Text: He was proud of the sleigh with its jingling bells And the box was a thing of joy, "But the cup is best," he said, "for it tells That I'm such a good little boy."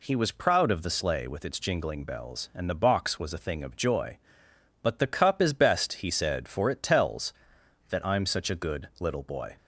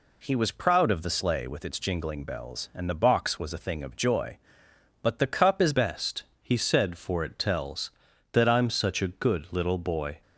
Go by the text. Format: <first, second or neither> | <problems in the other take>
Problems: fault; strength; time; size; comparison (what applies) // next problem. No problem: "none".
first | changes voice at "best"; from 5.7 s on; 4.5 s long